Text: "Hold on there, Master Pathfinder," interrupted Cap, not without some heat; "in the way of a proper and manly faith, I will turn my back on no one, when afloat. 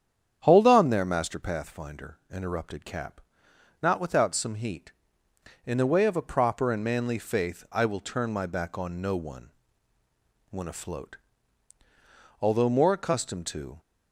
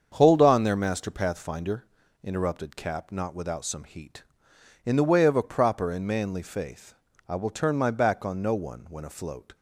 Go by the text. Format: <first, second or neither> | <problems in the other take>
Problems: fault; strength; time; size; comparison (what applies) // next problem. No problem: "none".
second | starts louder than the rest; strong; until 1.4 s; 8.5 dB; also in the second // goes on to say "Although more accustomed to"; from 12.3 s on; 1.4 s long